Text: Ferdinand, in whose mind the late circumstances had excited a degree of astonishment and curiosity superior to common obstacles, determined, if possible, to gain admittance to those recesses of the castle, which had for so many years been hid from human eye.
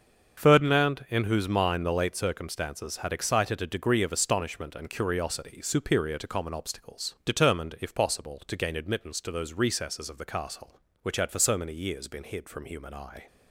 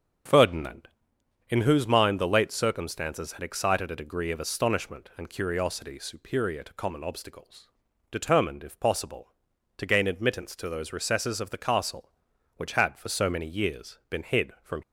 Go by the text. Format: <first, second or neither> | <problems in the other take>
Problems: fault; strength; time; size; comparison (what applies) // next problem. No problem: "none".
first | starts louder than the rest; until 1.8 s; 7 dB; also in the first // stops before "human eye"; at 14.8 s